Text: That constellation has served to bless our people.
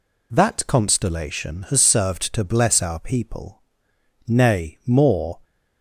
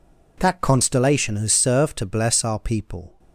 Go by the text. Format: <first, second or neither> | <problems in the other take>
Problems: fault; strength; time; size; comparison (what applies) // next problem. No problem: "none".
second | goes on to say "Nay more"; noticeable; from 4.2 s on; 1.1 s long